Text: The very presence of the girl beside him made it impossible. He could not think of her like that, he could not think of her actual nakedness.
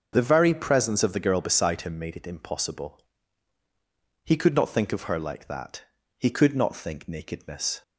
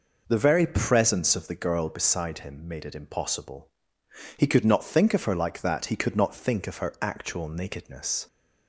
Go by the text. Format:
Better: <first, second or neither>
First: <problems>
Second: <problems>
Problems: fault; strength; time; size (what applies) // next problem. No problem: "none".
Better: second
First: starts louder than the rest; until 1.1 s; 6.5 dB // skips "of her actual"; at 7.0 s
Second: none